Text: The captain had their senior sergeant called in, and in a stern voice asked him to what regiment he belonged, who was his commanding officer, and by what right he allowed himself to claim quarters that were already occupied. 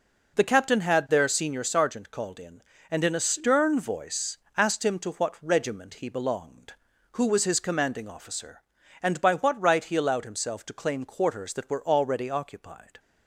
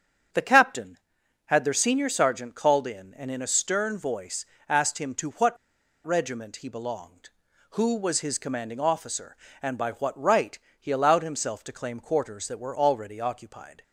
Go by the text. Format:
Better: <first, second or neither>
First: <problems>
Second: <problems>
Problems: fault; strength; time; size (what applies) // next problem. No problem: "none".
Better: first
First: pauses between "voice" and "asked"; slight; at 4.3 s; 0.20 s long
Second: starts louder than the rest; strong; until 1.8 s; 8 dB // pauses between "voice" and "asked"; slight; at 4.4 s; 0.24 s long // pauses between "what" and "regiment"; noticeable; at 5.5 s; 0.49 s long // pauses between "right" and "he"; slight; at 10.5 s; 0.22 s long